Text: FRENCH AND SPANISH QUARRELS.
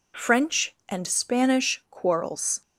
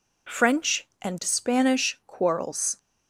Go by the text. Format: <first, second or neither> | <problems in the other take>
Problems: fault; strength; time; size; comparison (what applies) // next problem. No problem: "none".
neither | none